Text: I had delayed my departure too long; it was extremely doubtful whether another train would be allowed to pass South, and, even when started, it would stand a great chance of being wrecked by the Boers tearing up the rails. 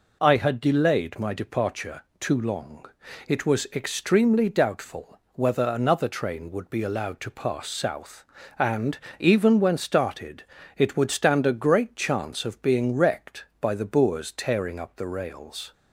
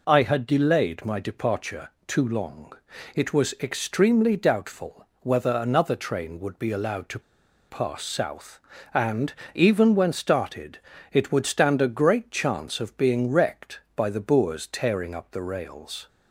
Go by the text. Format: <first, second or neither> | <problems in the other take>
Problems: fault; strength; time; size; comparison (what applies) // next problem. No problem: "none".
first | pauses between "departure" and "too"; slight; at 1.8 s; 0.20 s long; slight in the first // pauses between "to" and "pass"; noticeable; at 7.2 s; 0.48 s long